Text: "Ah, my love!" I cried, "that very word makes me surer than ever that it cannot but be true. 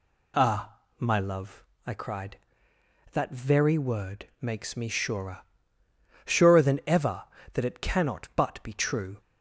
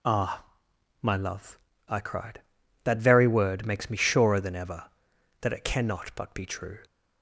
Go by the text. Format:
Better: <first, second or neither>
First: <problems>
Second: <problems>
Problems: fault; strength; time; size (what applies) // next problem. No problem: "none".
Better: second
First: says "surer" twice; at 6.2 s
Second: none